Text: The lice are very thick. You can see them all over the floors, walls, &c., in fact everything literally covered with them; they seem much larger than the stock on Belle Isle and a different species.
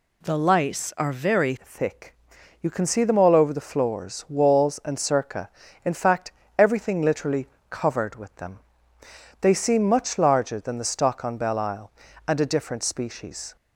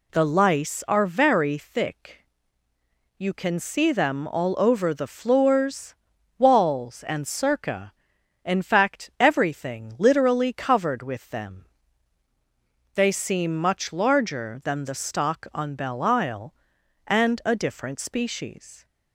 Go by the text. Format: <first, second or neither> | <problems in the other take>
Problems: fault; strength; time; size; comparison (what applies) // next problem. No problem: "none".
second | changes voice at "thick"; from 1.6 s on; 11.9 s long // pauses between "fact" and "everything"; slight; at 6.2 s; 0.30 s long // pauses between "literally" and "covered"; slight; at 7.4 s; 0.24 s long